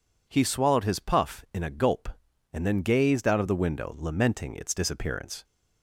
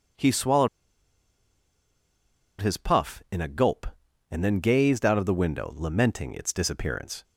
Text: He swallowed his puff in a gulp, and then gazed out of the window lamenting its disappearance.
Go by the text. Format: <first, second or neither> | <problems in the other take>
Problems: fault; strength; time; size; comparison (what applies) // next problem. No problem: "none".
first | pauses between "swallowed" and "his"; strong; at 0.6 s; 1.9 s long